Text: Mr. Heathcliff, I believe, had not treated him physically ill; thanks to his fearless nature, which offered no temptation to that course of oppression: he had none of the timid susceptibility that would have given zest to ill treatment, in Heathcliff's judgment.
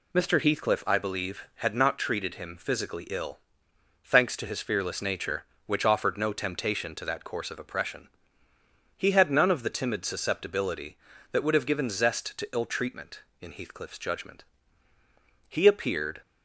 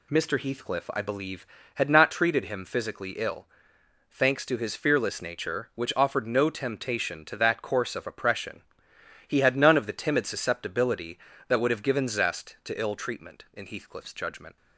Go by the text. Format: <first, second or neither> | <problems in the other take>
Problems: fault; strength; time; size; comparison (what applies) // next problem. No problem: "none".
second | goes on to say "He appeared"; noticeable; from 15.4 s on; 0.72 s long